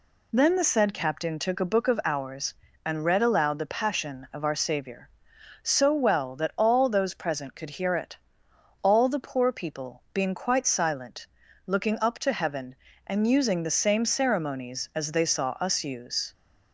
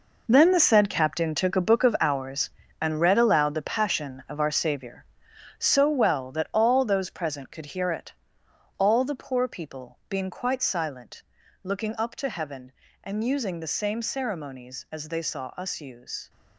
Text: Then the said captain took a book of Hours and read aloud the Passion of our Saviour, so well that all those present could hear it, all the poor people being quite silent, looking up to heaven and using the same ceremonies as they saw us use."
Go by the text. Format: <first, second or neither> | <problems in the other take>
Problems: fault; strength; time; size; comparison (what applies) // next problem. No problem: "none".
first | gets quieter; strong; throughout; 11.5 dB